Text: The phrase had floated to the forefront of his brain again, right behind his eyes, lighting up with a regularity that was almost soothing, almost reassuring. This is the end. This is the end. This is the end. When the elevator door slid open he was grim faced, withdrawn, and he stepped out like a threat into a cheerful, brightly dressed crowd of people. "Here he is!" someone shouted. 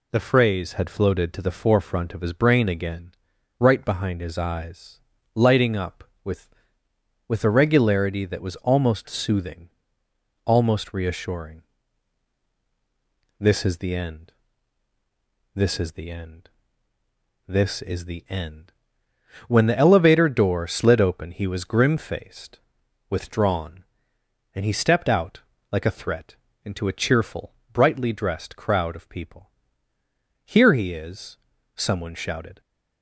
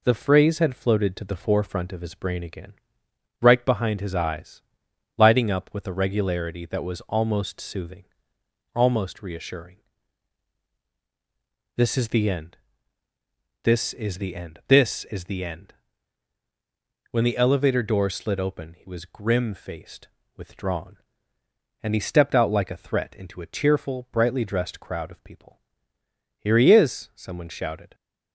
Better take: second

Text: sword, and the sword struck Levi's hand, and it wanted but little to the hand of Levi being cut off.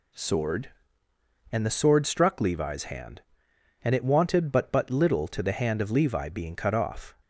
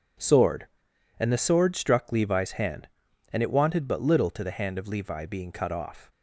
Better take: second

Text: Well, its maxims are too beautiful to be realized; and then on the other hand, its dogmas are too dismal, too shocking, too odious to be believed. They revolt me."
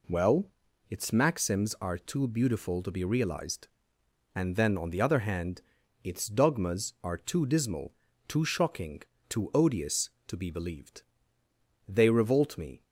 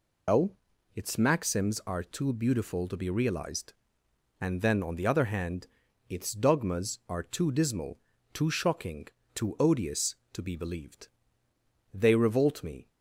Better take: first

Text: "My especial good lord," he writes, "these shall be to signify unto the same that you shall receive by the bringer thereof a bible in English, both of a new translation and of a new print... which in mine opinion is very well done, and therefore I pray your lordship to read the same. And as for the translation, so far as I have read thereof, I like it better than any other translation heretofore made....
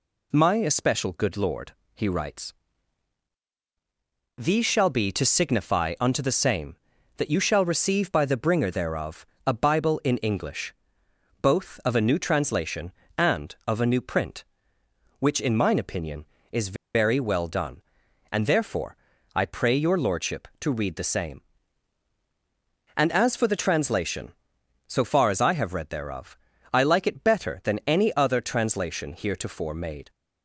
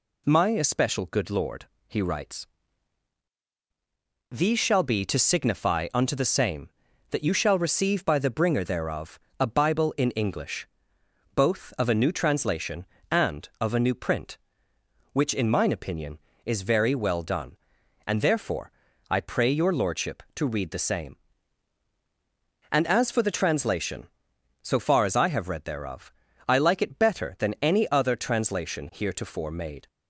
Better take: second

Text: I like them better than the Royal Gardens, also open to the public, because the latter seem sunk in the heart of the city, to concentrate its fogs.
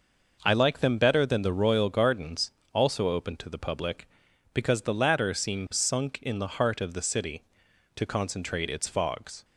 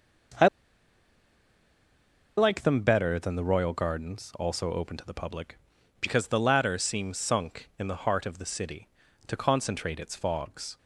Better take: first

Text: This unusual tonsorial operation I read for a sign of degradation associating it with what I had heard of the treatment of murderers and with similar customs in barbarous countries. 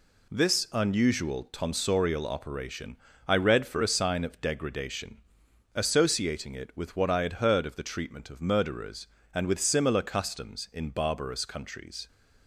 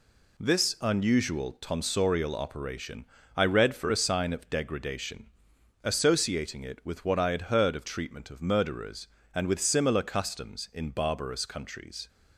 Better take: first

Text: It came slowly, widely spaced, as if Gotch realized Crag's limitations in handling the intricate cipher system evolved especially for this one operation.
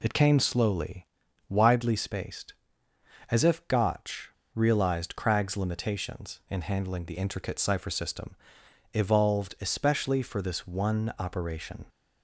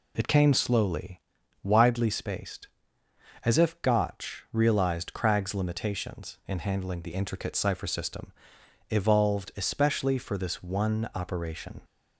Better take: second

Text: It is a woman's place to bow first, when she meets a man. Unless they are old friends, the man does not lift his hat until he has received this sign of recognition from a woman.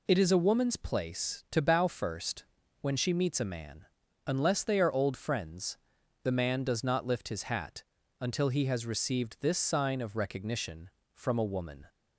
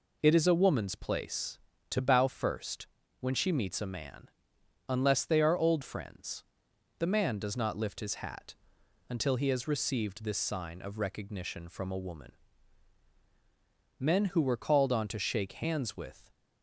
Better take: first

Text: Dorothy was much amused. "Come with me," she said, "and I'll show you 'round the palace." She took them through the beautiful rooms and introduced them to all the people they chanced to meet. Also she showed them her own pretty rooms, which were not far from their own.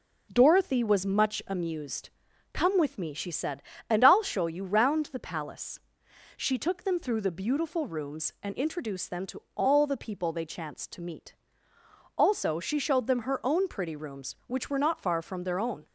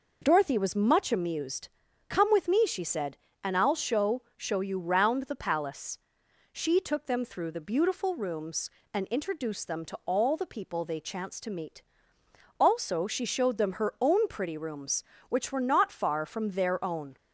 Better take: first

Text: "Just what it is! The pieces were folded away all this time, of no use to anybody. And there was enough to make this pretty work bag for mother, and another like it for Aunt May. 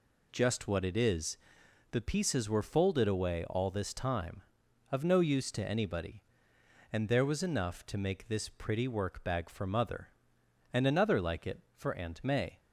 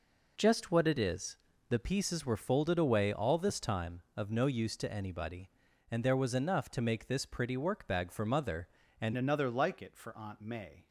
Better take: first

